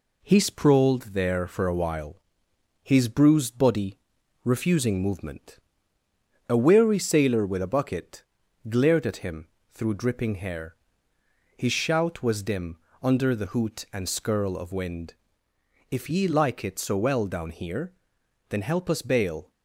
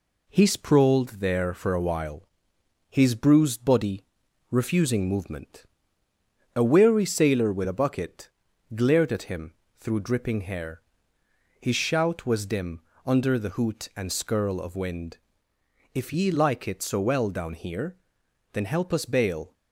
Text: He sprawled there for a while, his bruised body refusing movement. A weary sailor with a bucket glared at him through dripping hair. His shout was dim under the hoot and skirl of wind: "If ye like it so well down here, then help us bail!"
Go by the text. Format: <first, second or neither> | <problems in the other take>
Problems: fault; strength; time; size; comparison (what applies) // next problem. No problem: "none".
neither | pauses between "body" and "refusing"; noticeable; the same in both // pauses between "bucket" and "glared"; the same in both // pauses between "him" and "through"; slight; the same in both // pauses between "dim" and "under"; slight; the same in both